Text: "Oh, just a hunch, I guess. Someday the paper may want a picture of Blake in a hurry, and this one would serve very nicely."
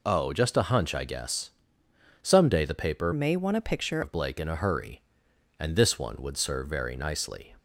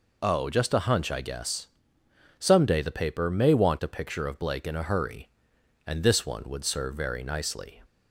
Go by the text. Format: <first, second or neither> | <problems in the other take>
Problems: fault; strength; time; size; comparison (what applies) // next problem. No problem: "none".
second | changes voice from "may" to "picture"; from 3.1 to 4.0 s; 0.9 s long